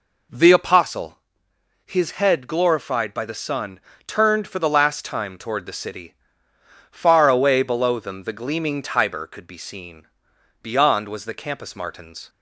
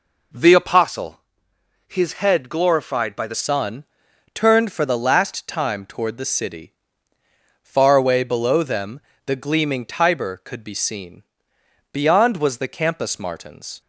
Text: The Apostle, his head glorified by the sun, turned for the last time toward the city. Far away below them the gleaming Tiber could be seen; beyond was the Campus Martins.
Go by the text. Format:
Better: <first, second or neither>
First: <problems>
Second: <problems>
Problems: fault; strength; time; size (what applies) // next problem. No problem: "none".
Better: first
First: none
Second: changes voice at "sun"; from 3.3 s on; 10.5 s long // pauses between "them" and "the"; slight; at 9.0 s; 0.24 s long